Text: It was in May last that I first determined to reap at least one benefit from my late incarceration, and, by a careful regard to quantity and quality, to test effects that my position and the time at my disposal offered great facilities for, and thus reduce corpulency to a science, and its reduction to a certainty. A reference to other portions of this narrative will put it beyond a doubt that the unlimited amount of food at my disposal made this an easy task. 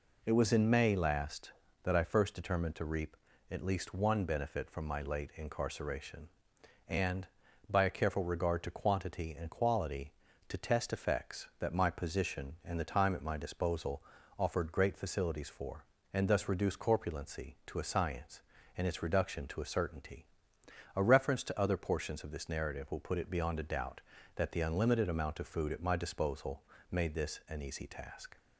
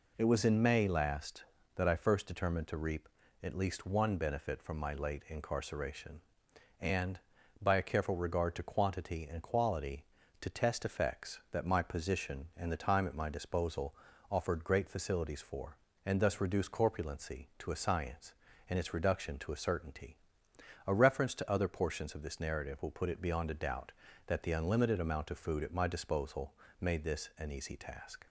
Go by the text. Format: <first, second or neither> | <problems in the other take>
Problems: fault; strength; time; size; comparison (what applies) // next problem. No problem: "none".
neither | pauses between "disposal" and "offered"; the same in both // pauses between "disposal" and "made"; slight; the same in both